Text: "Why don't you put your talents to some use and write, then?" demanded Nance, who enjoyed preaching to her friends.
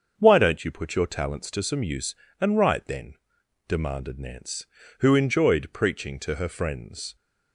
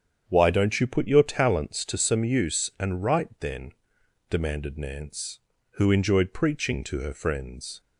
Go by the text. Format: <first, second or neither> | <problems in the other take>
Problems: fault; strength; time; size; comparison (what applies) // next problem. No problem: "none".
neither | starts louder than the rest; the same in both